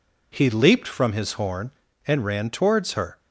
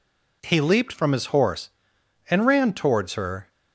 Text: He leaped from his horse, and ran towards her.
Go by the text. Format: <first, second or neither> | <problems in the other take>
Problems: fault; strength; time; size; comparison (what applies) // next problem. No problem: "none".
second | says "horn" for "horse"; at 1.3 s